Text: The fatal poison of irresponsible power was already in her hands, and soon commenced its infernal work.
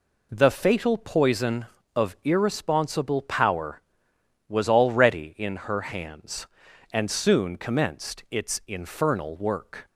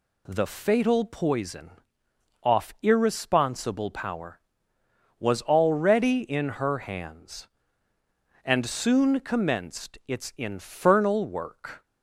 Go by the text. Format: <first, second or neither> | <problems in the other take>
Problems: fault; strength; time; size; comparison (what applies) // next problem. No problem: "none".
first | says "off" for "of"; at 2.4 s